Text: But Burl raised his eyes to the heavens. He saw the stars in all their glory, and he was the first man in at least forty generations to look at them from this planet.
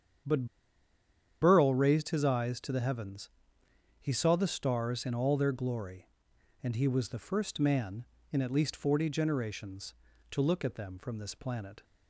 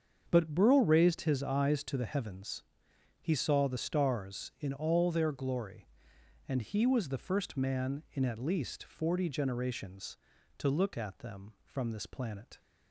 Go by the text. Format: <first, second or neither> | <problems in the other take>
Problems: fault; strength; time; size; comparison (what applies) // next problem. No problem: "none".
second | starts louder than the rest; strong; until 2.2 s; 8.5 dB; also in the second // pauses between "But" and "Burl"; noticeable; at 0.4 s; 0.96 s long